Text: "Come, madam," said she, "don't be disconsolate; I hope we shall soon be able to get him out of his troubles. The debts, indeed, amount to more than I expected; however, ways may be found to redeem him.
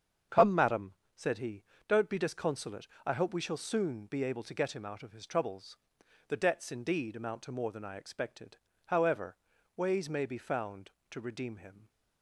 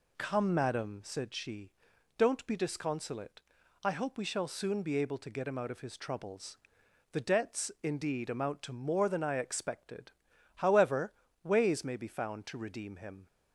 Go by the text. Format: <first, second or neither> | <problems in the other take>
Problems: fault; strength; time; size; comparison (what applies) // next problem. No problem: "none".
second | starts louder than the rest; strong; until 1.5 s; 7.5 dB // says "he" for "she"; at 1.3 s